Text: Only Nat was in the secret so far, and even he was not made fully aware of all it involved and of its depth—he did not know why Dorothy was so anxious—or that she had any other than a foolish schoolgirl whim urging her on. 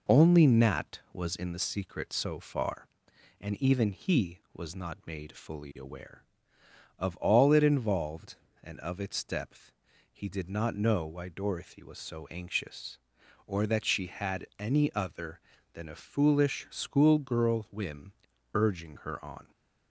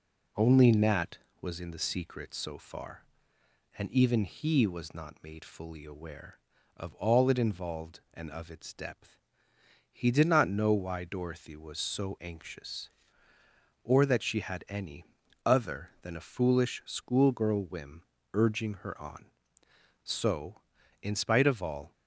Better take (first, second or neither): first